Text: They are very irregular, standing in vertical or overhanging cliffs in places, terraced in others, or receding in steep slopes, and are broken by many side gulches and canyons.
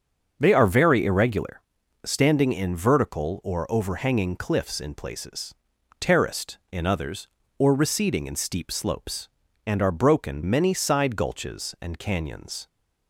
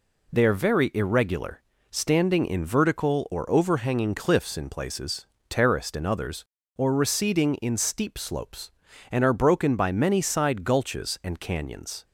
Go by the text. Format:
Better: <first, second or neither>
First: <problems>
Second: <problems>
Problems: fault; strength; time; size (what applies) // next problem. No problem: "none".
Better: second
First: starts louder than the rest; until 1.4 s; 6.5 dB // skips "by"; at 10.4 s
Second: none